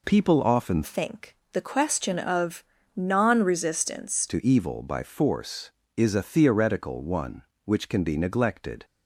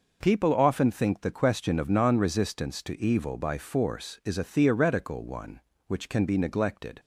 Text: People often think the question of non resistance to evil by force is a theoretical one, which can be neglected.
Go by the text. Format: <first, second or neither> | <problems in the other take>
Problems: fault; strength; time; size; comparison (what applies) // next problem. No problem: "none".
second | changes voice from "think" to "resistance"; from 0.8 to 4.2 s; 3.4 s long // pauses between "think" and "the"; slight; at 1.3 s; 0.16 s long // pauses between "of" and "non"; slight; at 2.6 s; 0.32 s long